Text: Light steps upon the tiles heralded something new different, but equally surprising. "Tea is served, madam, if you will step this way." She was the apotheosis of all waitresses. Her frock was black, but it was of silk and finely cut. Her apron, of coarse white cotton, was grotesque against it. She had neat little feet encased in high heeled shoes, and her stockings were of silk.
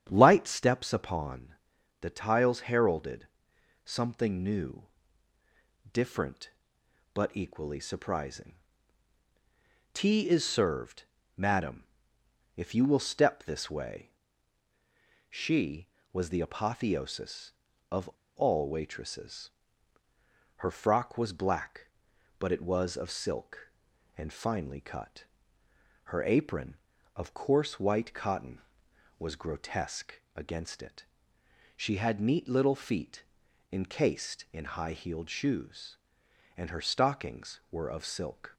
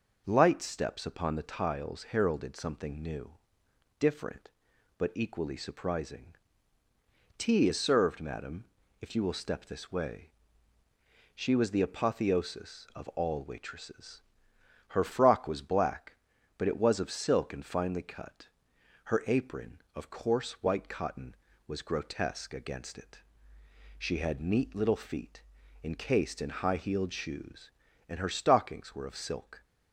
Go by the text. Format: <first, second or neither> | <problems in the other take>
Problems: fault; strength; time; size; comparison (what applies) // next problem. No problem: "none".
second | starts louder than the rest; strong; until 1.1 s; 8.5 dB // pauses between "upon" and "the"; noticeable; at 1.4 s; 0.52 s long // pauses between "heralded" and "something"; noticeable; at 3.2 s; 0.56 s long // pauses between "new" and "different"; at 4.8 s; 1.0 s long; noticeable in the second // pauses between "of" and "all"; slight; at 18.0 s; 0.28 s long // pauses between "grotesque" and "against"; slight; at 30.1 s; 0.16 s long // pauses between "feet" and "encased"; noticeable; at 33.2 s; 0.48 s long; also in the second